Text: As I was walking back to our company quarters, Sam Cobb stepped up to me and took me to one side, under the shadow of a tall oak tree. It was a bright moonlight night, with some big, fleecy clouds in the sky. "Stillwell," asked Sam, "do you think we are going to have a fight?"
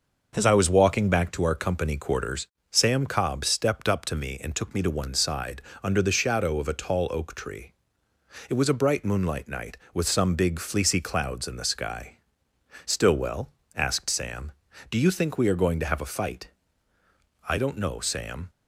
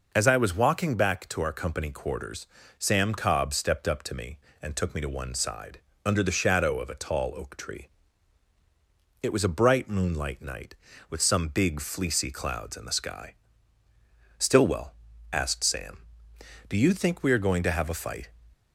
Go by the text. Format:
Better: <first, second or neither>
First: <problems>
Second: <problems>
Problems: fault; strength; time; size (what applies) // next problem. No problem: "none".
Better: second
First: starts louder than the rest; noticeable; until 1.4 s; 6 dB // goes on to say "I don't know Sam"; noticeable; from 17.4 s on; 1.0 s long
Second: none